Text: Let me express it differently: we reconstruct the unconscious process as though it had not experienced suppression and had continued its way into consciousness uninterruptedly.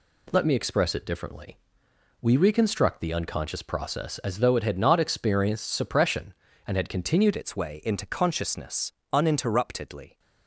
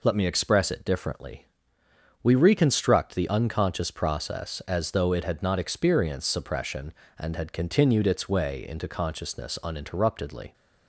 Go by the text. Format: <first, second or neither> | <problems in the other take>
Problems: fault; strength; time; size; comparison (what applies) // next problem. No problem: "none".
second | changes voice at "its"; from 7.3 s on; 2.8 s long // pauses between "consciousness" and "uninterruptedly"; slight; at 8.9 s; 0.18 s long